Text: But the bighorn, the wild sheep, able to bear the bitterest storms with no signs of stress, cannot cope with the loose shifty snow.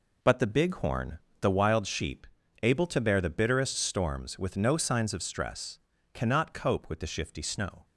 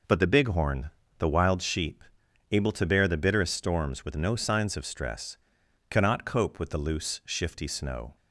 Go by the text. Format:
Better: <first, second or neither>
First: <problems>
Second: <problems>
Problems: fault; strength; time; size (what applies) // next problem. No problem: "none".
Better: second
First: skips "loose"; at 7.0 s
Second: none